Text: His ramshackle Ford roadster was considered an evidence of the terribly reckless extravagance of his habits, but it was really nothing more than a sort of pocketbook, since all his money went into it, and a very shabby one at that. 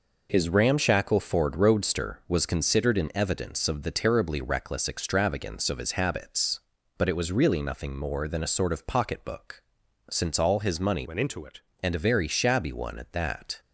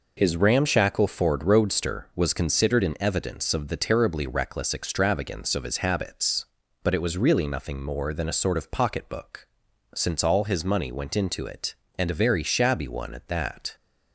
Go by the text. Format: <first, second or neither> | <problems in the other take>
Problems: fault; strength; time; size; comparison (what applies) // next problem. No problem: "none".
second | changes voice from "went" to "it"; from 11.0 to 11.6 s; 0.6 s long